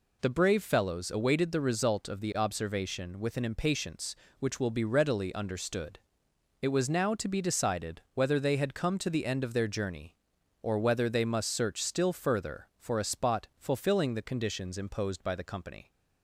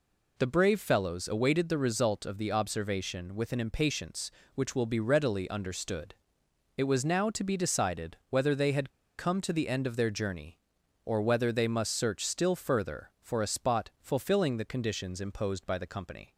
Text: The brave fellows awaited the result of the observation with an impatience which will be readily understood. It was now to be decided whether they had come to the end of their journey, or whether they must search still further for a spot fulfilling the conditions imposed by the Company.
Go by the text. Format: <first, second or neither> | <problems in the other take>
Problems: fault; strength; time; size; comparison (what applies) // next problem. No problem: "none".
first | pauses between "had" and "come"; slight; at 8.9 s; 0.27 s long